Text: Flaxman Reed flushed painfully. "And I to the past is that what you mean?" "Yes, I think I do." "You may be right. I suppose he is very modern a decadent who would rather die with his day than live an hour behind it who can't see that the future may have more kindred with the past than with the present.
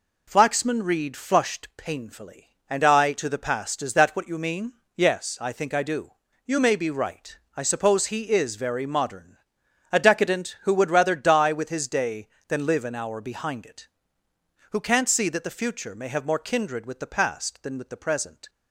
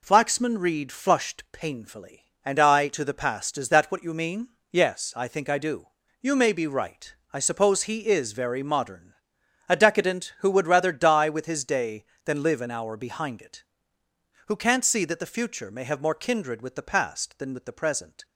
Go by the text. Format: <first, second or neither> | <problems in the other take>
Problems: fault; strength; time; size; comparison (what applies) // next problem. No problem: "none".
neither | pauses between "modern" and "a"; noticeable; the same in both